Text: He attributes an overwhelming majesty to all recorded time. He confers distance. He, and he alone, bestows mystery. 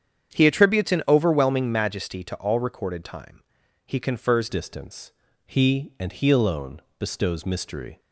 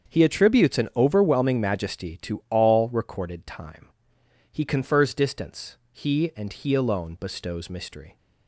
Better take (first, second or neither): second